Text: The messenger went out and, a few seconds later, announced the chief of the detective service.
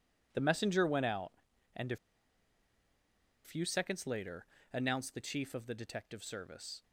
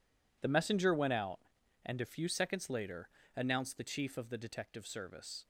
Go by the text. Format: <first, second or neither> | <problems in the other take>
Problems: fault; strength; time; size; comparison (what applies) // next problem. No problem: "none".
second | pauses between "a" and "few"; strong; at 1.9 s; 1.4 s long